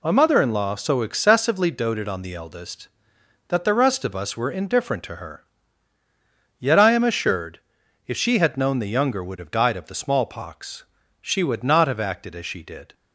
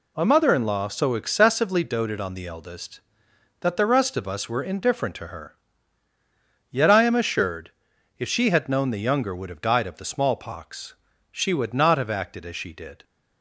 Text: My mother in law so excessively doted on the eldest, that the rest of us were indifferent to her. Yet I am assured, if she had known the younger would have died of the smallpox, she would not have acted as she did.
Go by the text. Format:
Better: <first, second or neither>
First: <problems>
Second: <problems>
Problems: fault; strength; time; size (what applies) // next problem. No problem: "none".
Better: neither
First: none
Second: none